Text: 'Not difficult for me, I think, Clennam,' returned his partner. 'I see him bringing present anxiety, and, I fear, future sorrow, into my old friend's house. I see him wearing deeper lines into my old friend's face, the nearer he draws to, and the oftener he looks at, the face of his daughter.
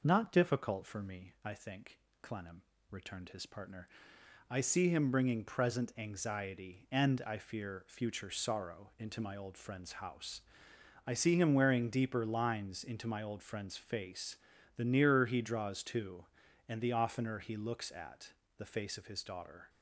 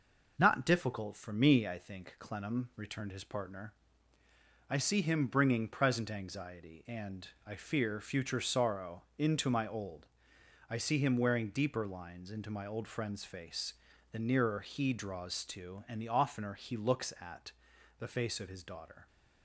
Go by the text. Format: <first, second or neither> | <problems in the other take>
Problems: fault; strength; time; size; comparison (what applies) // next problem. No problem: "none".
first | skips "friend's house"; at 10.3 s